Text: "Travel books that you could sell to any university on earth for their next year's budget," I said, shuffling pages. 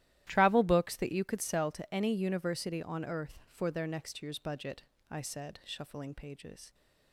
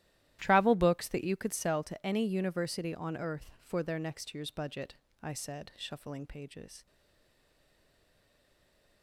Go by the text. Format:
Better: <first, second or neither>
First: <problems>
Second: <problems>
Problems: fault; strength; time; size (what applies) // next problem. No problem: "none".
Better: first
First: starts louder than the rest; strong; until 1.2 s; 13.5 dB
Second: starts louder than the rest; strong; until 1.4 s; 13.5 dB // stays silent after the last word; from 6.8 s on; 2.2 s long